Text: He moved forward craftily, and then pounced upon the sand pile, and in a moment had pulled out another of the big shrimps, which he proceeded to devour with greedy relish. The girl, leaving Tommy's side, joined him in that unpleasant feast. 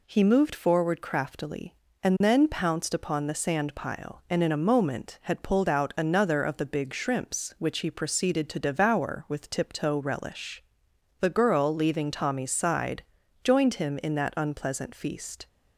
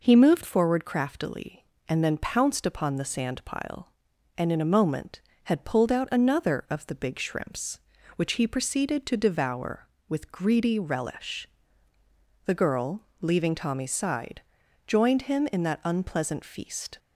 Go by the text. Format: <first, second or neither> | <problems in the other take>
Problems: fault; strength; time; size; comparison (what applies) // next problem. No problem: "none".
second | says "tiptoe" for "greedy"; at 9.4 s